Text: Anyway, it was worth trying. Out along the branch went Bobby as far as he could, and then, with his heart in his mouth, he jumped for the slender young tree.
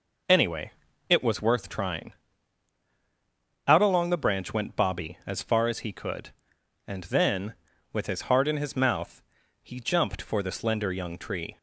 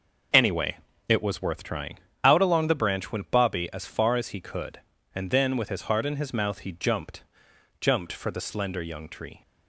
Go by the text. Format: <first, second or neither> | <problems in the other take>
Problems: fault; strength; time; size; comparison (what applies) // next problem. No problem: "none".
first | says "jumped" twice; at 7.8 s